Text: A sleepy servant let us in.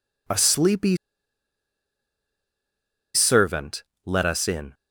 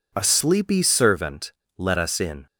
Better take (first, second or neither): second